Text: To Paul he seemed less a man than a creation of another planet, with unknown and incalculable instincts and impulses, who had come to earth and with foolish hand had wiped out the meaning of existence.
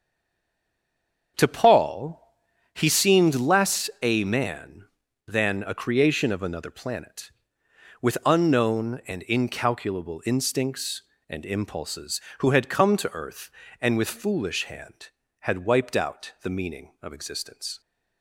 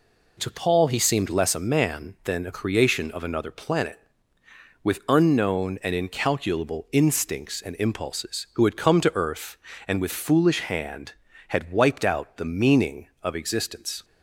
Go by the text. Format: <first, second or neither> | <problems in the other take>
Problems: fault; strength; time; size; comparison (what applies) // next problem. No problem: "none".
second | stays silent before the first word; noticeable; until 1.3 s; 1.3 s long // starts louder than the rest; strong; until 2.9 s; 7 dB // pauses between "Paul" and "he"; noticeable; at 2.1 s; 0.56 s long